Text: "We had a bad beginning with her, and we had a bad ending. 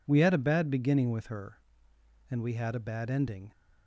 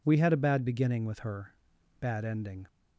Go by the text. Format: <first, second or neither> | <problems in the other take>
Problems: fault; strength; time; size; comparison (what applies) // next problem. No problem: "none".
first | skips "and we had a"; at 1.7 s